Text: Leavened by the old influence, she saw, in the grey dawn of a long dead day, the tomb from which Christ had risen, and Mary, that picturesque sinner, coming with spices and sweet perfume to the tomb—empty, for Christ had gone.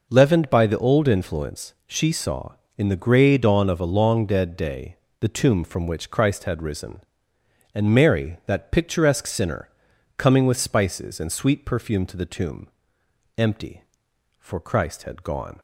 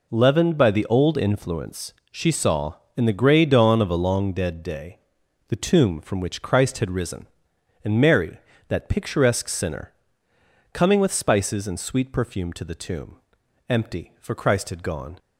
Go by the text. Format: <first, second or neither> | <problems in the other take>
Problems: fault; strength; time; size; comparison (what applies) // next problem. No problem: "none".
neither | none